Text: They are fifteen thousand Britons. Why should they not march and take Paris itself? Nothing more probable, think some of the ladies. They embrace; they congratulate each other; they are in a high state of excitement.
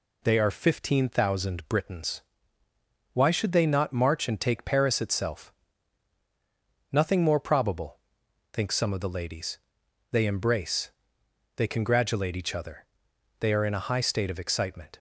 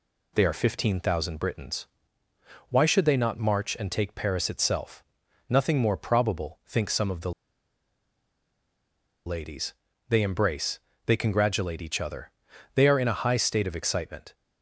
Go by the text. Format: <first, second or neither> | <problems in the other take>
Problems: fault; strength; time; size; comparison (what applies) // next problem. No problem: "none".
first | pauses between "the" and "ladies"; strong; at 7.3 s; 1.9 s long